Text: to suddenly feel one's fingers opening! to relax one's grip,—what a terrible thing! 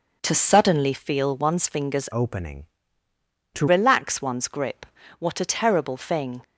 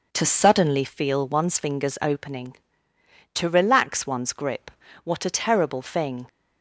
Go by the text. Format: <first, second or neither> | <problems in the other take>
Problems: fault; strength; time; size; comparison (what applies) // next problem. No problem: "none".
second | changes voice from "opening" to "to"; from 2.1 to 3.6 s; 1.5 s long